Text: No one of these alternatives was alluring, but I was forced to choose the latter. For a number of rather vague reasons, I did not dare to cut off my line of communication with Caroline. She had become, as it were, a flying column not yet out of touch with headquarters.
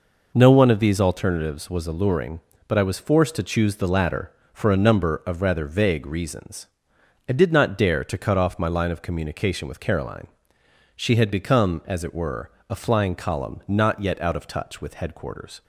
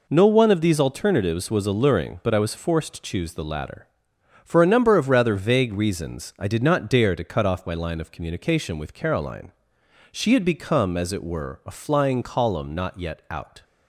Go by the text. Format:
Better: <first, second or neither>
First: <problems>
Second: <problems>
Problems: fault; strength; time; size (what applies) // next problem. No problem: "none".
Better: first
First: none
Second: stops before "of touch with headquarters"; at 13.6 s